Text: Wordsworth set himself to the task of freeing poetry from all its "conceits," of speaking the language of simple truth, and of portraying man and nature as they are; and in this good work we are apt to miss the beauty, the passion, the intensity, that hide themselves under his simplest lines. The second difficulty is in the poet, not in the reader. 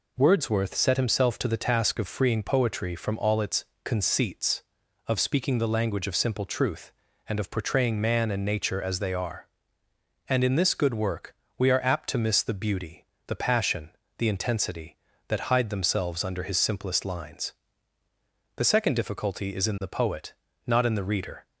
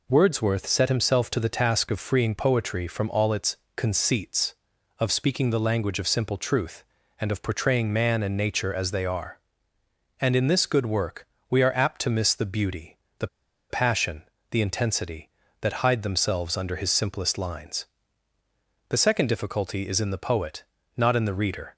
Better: first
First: pauses between "its" and "conceits"; slight; at 3.6 s; 0.18 s long // pauses between "work" and "we"; slight; at 11.3 s; 0.24 s long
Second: pauses between "its" and "conceits"; slight; at 3.5 s; 0.18 s long // pauses between "work" and "we"; slight; at 11.2 s; 0.24 s long // pauses between "the" and "passion"; at 13.2 s; 0.43 s long

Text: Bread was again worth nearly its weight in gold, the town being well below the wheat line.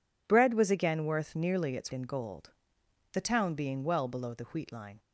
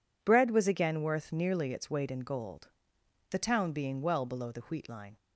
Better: second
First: skips "weight"; at 1.9 s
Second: none

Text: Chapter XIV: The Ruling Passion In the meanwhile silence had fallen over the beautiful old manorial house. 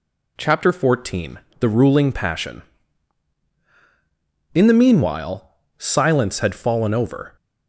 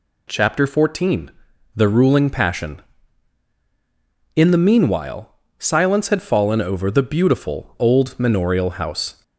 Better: second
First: pauses between "meanwhile" and "silence"; slight; at 5.4 s; 0.28 s long // stops before "the beautiful old manorial house"; at 7.3 s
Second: pauses between "meanwhile" and "silence"; slight; at 5.3 s; 0.26 s long

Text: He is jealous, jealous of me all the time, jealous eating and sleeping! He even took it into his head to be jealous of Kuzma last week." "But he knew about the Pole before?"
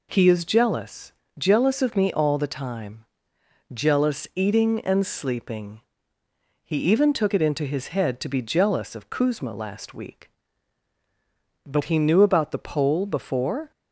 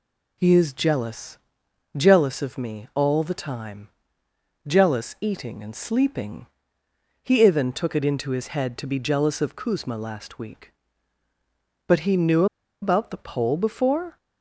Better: first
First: none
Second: pauses between "knew" and "about"; at 12.4 s; 0.37 s long

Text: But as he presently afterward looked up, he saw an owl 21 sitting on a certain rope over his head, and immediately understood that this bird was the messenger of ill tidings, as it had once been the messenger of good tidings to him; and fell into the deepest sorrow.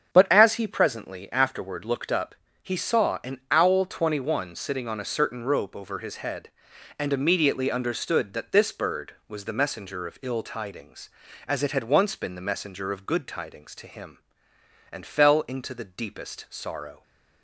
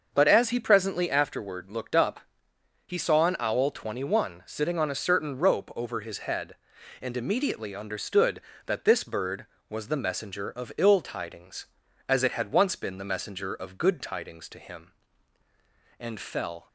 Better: first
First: starts louder than the rest; strong; until 1.1 s; 8 dB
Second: starts louder than the rest; until 1.1 s; 6.5 dB // stops before "into the deepest sorrow"; at 16.6 s

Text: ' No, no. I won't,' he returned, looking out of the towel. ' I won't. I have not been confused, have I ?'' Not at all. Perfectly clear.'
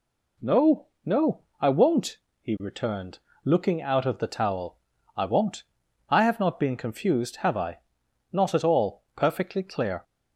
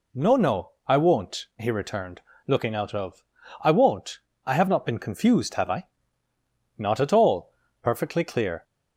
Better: first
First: none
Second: skips "the towel"; at 3.3 s

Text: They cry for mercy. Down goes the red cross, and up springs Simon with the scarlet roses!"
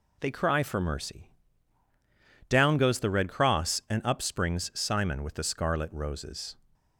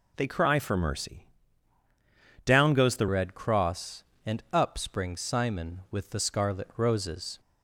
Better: first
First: none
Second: changes voice at "red"; from 3.0 s on; 4.3 s long

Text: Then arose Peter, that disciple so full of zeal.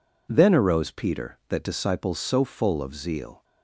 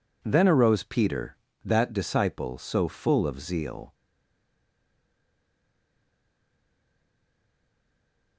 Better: first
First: none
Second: stays silent after the last word; strong; from 3.9 s on; 4.4 s long

